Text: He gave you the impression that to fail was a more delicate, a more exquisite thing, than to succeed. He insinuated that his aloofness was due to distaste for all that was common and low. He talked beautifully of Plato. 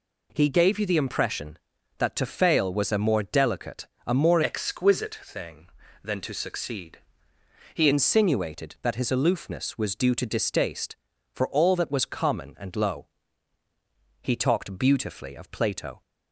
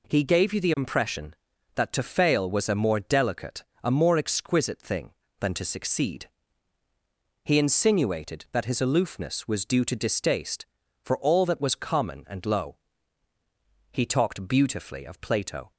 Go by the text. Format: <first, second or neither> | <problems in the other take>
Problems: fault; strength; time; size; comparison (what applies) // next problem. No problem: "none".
second | changes voice from "exquisite" to "He"; from 4.4 to 7.8 s; 3.4 s long